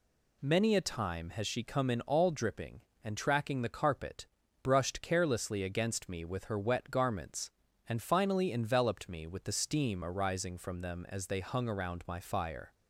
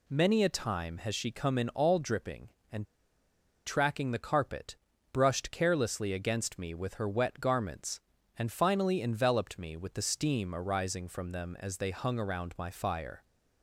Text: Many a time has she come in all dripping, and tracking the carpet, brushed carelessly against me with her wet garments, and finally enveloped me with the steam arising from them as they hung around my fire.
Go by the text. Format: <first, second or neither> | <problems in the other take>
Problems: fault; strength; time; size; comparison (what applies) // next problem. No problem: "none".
first | pauses between "and" and "tracking"; noticeable; at 2.8 s; 0.80 s long